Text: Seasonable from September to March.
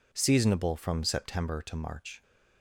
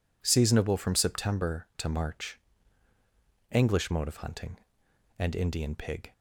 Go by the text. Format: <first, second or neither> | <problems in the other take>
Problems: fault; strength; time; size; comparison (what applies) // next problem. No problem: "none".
first | goes on to say "ENGLISH MODE OF HUNTING AND INDIAN PIG"; strong; from 3.5 s on; 2.6 s long